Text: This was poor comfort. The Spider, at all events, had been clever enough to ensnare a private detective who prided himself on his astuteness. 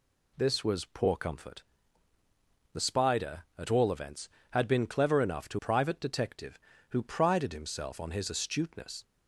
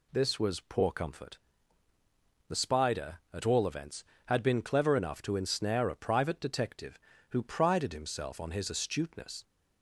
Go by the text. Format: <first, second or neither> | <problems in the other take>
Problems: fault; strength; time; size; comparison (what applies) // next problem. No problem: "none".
second | skips "ensnare a"; at 5.5 s